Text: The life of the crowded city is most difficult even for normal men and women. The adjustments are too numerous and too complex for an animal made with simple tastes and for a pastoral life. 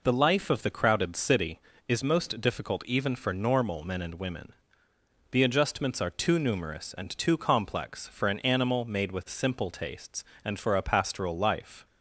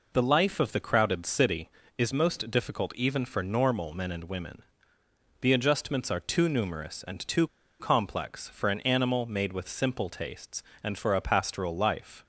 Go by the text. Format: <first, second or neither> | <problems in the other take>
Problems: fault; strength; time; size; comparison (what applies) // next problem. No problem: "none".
first | pauses between "too" and "complex"; slight; at 7.4 s; 0.33 s long